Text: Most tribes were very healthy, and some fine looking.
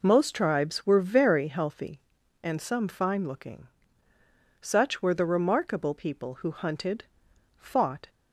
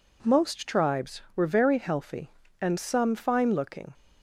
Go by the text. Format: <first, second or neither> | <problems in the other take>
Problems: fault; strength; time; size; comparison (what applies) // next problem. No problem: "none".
second | goes on to say "Such were the remarkable people who hunted fought"; strong; from 4.6 s on; 3.4 s long